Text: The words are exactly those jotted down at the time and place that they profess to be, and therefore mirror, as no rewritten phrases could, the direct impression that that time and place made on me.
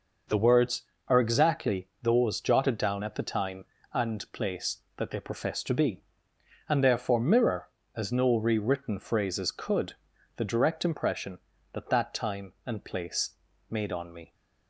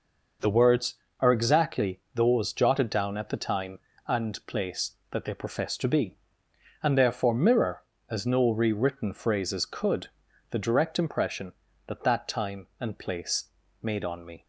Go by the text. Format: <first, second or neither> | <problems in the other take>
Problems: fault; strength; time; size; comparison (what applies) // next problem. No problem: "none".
neither | pauses between "place" and "made"; slight; the same in both